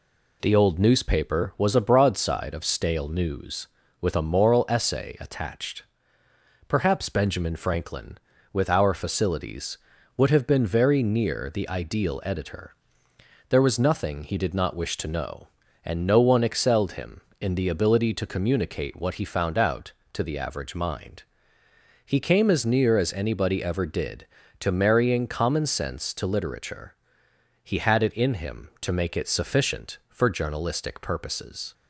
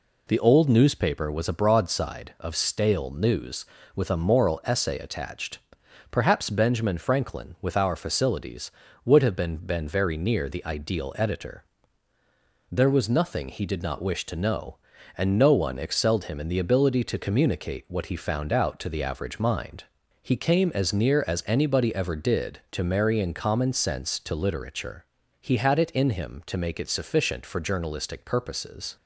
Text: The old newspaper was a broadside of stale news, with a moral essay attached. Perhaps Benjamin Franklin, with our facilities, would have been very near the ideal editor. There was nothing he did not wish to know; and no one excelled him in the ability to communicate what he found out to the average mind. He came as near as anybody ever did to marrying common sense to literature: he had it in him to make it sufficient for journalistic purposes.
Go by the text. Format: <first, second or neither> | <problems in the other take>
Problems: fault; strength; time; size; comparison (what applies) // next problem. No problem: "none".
first | says "been" twice; at 9.5 s